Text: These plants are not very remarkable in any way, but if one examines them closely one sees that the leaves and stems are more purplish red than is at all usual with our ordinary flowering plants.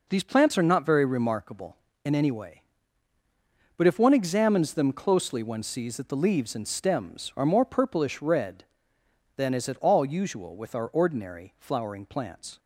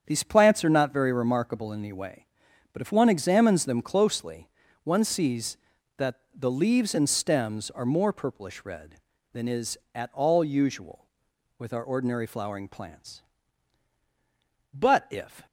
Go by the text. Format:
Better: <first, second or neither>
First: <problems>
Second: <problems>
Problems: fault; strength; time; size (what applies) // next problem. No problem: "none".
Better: first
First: none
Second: starts louder than the rest; strong; until 1.0 s; 8 dB // pauses between "closely" and "one"; slight; at 4.4 s; 0.36 s long // pauses between "that" and "the"; slight; at 6.1 s; 0.18 s long // goes on to say "But if"; noticeable; from 14.7 s on; 0.74 s long